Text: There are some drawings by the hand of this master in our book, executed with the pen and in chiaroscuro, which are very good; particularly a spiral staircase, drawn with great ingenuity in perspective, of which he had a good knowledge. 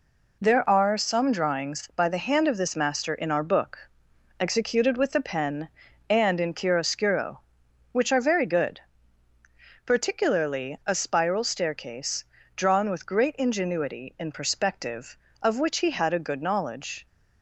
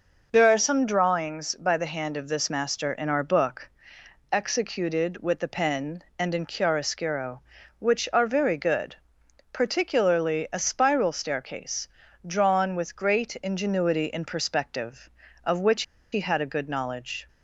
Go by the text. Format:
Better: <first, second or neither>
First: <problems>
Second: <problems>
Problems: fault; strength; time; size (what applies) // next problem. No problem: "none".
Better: first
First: none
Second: pauses between "which" and "he"; slight; at 15.8 s; 0.30 s long